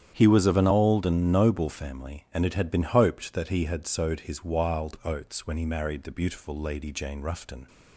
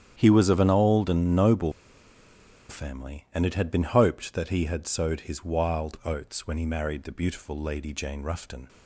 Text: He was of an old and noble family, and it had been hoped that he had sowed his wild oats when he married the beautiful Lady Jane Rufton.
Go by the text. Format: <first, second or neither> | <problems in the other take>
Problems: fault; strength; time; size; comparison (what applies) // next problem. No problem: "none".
first | starts louder than the rest; strong; until 1.1 s; 9.5 dB; strong in the first // pauses between "noble" and "family"; noticeable; at 1.7 s; 0.97 s long